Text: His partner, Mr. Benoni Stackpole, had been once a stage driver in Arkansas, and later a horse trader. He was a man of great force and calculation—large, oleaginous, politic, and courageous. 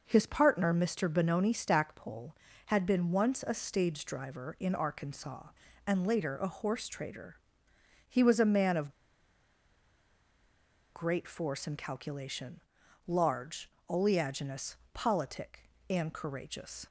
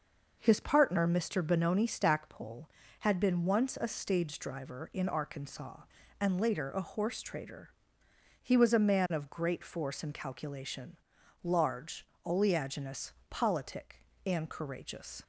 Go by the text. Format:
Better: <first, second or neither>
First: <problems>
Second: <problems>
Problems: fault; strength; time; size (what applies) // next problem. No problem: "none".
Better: second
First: pauses between "of" and "great"; strong; at 8.9 s; 2.0 s long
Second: none